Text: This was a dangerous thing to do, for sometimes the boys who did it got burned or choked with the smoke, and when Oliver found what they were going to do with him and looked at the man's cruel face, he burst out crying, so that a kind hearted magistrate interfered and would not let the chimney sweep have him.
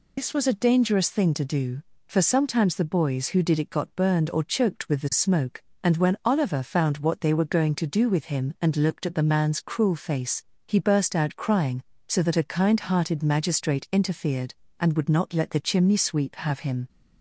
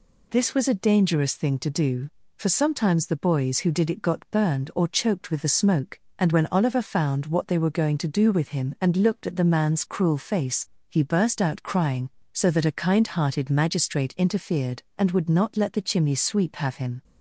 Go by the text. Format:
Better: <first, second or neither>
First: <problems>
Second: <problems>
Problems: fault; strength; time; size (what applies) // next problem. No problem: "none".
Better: second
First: loses the start of "This"; at 0.1 s; 80 ms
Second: none